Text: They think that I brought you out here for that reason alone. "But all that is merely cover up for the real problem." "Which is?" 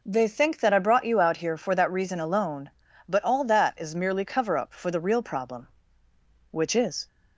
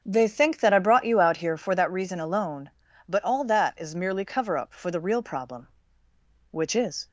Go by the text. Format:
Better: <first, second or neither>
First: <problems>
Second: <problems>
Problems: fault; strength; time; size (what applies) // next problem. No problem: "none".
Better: first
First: none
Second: starts louder than the rest; until 1.9 s; 7 dB